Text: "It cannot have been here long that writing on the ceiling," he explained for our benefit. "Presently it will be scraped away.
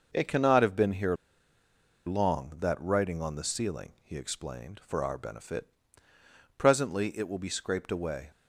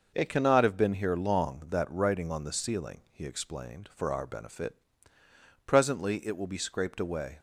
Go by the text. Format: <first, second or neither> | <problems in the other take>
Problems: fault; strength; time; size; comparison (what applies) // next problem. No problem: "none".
second | pauses between "here" and "long"; noticeable; at 1.1 s; 0.90 s long